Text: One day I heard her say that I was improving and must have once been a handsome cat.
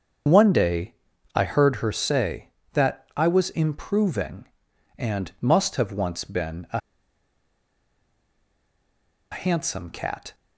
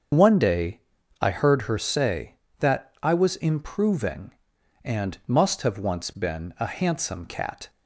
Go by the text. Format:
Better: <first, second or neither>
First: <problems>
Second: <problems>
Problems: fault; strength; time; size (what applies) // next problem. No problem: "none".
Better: second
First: starts louder than the rest; strong; until 1.6 s; 7 dB // pauses between "day" and "I"; at 0.9 s; 0.40 s long // pauses between "a" and "handsome"; strong; at 6.7 s; 2.5 s long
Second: starts louder than the rest; strong; until 1.5 s; 7 dB // pauses between "day" and "I"; at 0.8 s; 0.40 s long